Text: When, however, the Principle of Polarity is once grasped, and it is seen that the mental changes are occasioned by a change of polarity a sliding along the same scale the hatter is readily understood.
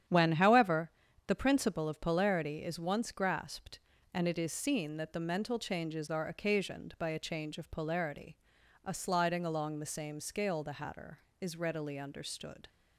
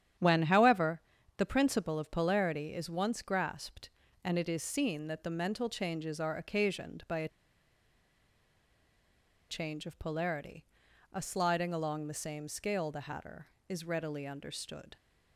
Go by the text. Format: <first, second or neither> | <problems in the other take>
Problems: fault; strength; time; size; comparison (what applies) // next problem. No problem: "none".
first | starts louder than the rest; strong; until 1.5 s; 9.5 dB; strong in the first // pauses between "a" and "change"; strong; at 7.2 s; 2.2 s long // pauses between "polarity" and "a"; noticeable; at 10.6 s; 0.52 s long; noticeable in the first